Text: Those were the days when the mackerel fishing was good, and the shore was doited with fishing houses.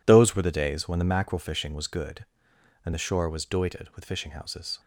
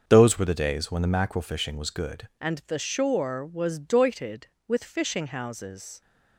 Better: first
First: none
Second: starts louder than the rest; until 1.0 s; 6.5 dB // changes voice at "and"; from 2.4 s on; 3.6 s long

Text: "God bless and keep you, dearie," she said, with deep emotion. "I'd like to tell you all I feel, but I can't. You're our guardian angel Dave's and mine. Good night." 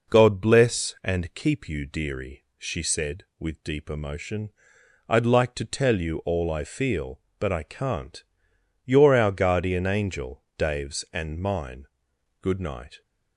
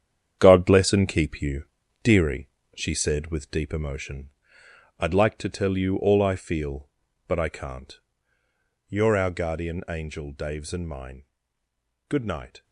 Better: first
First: none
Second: gets quieter; strong; throughout; 8 dB

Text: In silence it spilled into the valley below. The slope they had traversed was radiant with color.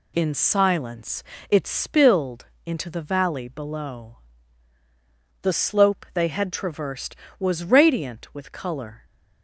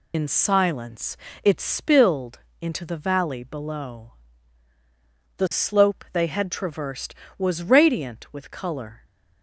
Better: first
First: pauses between "silence" and "it"; slight; at 1.2 s; 0.26 s long // pauses between "spilled" and "into"; slight; at 2.4 s; 0.22 s long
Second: loses the start of "In"; at 0.1 s; 60 ms // pauses between "silence" and "it"; slight; at 1.1 s; 0.26 s long // pauses between "spilled" and "into"; slight; at 2.3 s; 0.24 s long

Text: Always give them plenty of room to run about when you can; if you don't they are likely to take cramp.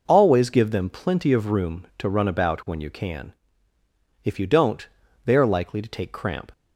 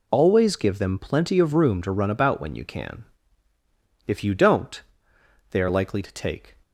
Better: first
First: pauses between "don't" and "they"; at 4.8 s; 0.38 s long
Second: pauses between "don't" and "they"; noticeable; at 4.8 s; 0.68 s long // stops before "cramp"; at 6.6 s

